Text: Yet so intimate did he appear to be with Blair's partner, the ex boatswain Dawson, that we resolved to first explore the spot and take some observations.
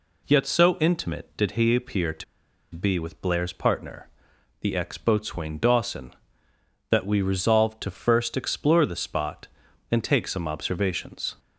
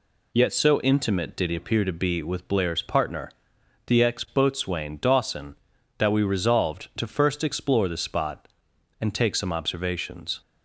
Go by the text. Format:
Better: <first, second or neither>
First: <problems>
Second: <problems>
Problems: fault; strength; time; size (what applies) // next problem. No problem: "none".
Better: second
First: pauses between "to" and "be"; noticeable; at 2.2 s; 0.50 s long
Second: none